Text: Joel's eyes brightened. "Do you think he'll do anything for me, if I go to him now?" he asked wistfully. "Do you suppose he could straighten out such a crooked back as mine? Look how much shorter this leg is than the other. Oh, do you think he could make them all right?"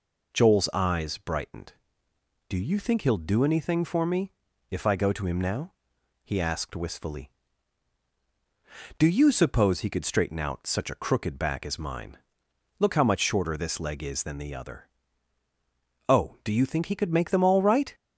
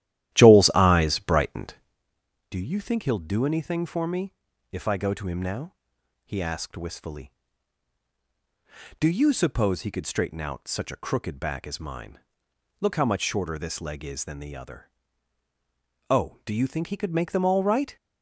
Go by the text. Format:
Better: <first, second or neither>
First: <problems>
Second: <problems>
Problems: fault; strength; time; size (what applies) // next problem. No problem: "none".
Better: first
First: none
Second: starts louder than the rest; strong; until 2.0 s; 13 dB